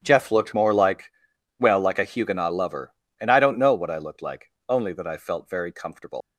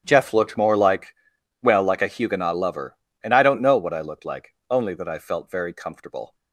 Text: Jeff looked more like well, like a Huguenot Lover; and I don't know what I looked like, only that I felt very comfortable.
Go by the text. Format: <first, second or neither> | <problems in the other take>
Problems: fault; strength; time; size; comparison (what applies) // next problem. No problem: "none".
second | starts louder than the rest; strong; until 1.0 s; 10 dB; strong in the second // pauses between "like" and "well"; noticeable; at 1.1 s; 0.48 s long; noticeable in the second // leaves "comfortable" unfinished; at 6.2 s; 130 ms